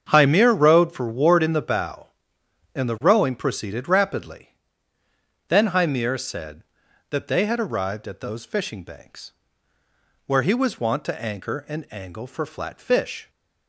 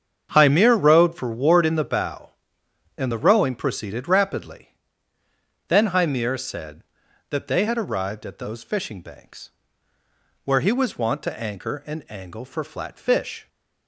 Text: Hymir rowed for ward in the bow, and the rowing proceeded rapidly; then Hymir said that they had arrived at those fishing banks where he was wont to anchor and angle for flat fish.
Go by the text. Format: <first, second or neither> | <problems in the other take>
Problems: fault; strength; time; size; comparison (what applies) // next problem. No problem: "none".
neither | starts louder than the rest; strong; the same in both // pauses between "banks" and "where"; noticeable; the same in both